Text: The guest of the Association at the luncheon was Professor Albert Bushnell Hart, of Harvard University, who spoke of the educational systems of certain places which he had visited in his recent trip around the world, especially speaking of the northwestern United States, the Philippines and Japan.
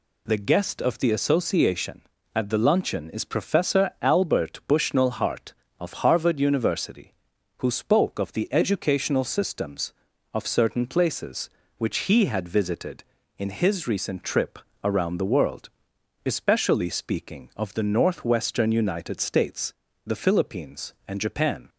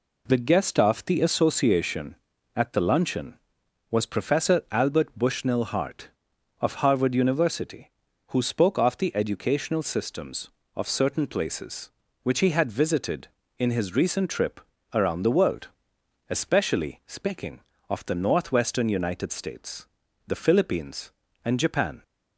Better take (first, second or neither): second